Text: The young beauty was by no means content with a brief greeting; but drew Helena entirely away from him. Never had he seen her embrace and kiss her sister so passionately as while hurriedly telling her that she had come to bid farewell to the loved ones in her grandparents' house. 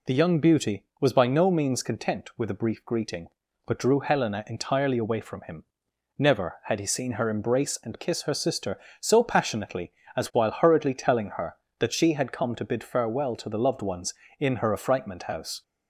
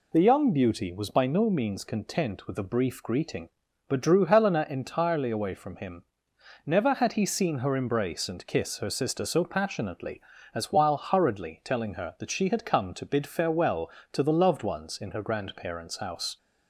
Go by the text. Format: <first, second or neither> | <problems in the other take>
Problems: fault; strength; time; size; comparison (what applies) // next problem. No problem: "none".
second | says "affrightment" for "grandparents"; at 14.7 s